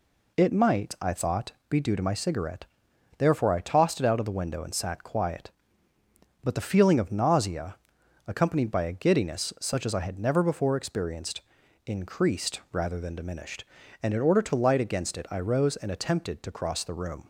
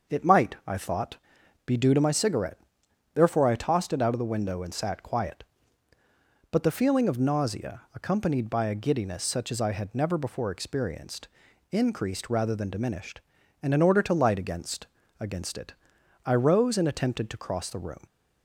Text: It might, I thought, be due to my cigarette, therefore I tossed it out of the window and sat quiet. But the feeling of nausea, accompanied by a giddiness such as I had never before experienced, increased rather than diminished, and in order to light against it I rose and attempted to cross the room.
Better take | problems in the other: first | starts louder than the rest; until 1.7 s; 6 dB // says "against" twice; at 15.1 s // pauses between "it" and "I"; noticeable; at 15.7 s; 0.50 s long

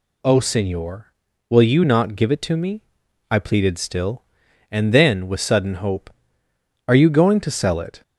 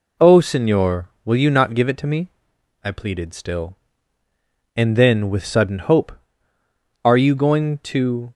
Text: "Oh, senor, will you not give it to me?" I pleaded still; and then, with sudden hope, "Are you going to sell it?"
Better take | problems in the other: first | stops before "sell it"; at 8.2 s

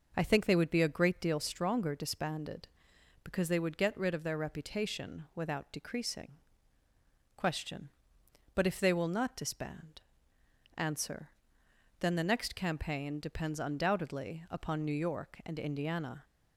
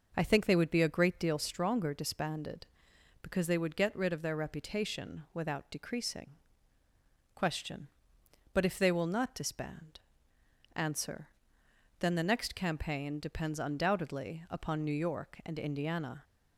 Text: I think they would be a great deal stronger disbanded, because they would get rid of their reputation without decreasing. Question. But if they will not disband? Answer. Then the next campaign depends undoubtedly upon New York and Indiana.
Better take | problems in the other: neither | none

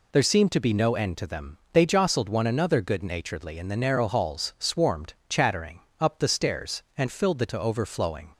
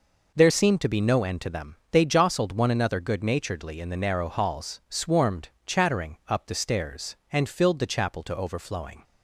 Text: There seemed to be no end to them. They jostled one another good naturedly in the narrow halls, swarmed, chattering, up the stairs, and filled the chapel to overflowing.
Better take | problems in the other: second | skips "chapel"; at 7.4 s

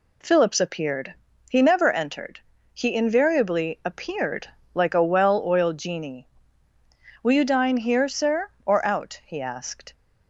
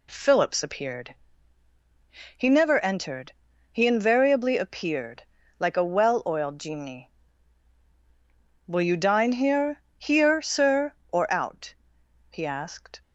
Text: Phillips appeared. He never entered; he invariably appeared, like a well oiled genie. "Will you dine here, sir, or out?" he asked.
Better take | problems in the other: first | says "here" twice; at 9.9 s

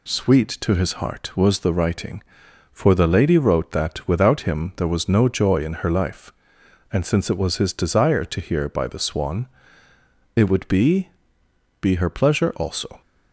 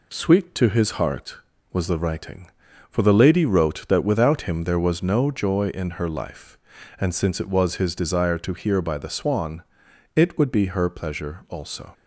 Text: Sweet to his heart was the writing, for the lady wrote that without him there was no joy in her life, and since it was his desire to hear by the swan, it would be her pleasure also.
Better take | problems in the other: second | says "be" twice; at 11.8 s

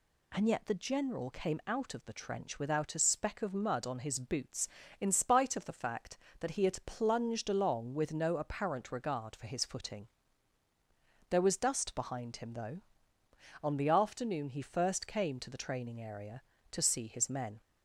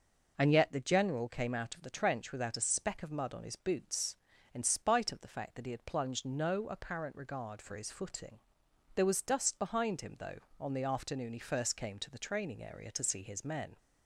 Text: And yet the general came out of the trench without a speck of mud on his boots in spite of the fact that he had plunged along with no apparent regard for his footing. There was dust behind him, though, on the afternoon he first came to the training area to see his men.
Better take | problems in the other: first | skips "along with"; at 6.2 s

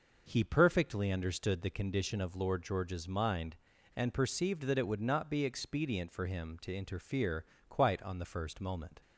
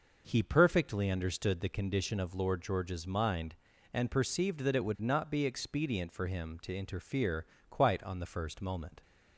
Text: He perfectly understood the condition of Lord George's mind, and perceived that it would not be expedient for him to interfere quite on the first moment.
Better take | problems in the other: neither | pauses between "interfere" and "quite"; slight; the same in both

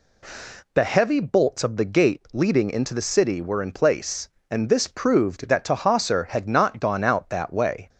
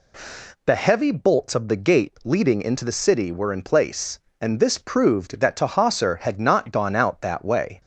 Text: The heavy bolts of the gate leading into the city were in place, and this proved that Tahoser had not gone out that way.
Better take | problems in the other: neither | none

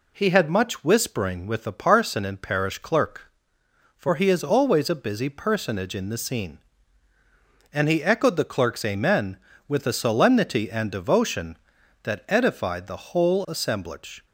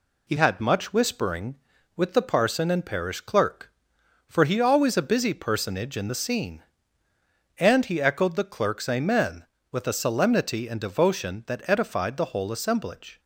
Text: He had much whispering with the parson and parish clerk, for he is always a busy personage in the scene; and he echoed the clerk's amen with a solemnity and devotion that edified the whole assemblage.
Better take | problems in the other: first | skips "is"; at 4.5 s

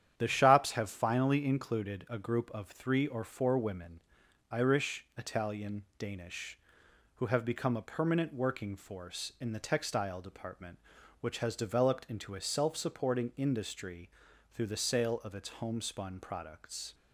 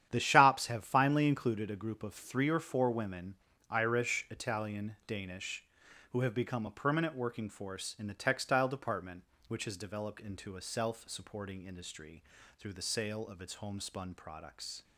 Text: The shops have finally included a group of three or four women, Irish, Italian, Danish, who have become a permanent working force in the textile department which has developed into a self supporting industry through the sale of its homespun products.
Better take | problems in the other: neither | starts louder than the rest; strong; the same in both // pauses between "industry" and "through"; the same in both

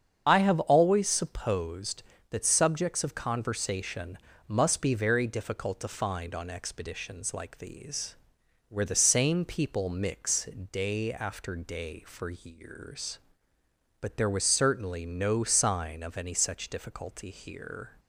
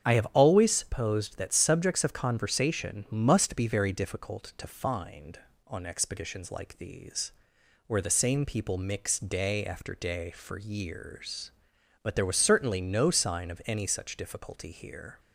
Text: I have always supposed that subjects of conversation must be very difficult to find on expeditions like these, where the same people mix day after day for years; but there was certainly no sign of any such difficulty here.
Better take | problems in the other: second | loses the start of "I"; at 0.2 s; 30 ms // starts louder than the rest; strong; until 1.2 s; 7.5 dB; strong in the second // pauses between "conversation" and "must"; slight; at 4.1 s; 0.30 s long // pauses between "mix" and "day"; slight; at 10.4 s; 0.26 s long

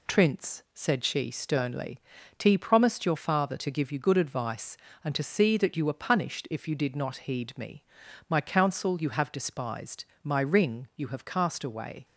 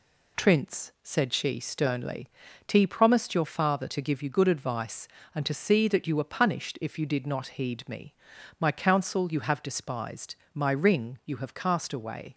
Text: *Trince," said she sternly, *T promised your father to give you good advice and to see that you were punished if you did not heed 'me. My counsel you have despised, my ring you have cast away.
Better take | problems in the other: neither | none

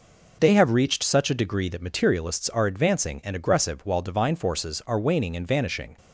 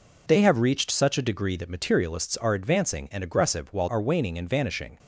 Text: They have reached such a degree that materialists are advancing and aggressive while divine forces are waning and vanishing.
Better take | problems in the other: first | skips "divine forces"; at 3.8 s

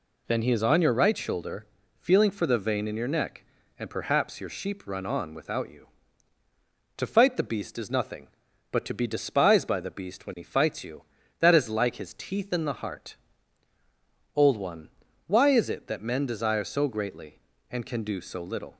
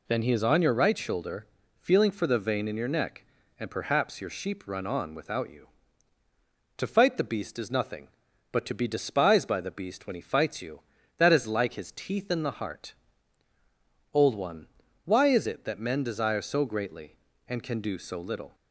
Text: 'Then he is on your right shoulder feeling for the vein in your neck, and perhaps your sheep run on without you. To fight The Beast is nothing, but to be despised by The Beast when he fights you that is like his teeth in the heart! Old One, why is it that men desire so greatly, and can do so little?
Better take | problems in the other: neither | pauses between "shoulder" and "feeling"; slight; the same in both

